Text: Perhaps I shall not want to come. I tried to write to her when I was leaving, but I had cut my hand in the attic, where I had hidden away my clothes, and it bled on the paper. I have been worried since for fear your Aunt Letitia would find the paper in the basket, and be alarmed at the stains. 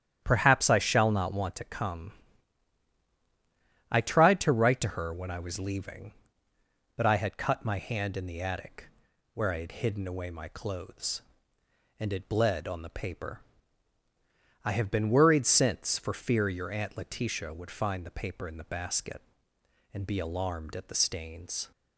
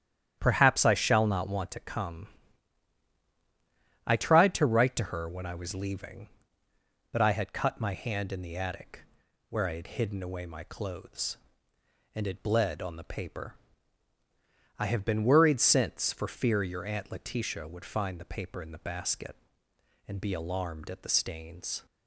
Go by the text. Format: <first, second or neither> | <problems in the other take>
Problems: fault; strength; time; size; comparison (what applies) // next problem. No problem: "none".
neither | starts louder than the rest; strong; the same in both